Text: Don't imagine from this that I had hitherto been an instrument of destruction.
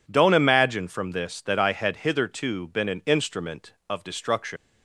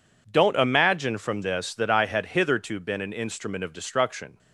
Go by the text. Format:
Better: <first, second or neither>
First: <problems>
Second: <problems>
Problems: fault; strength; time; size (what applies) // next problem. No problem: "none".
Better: second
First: leaves "destruction" unfinished; at 4.5 s; 115 ms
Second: none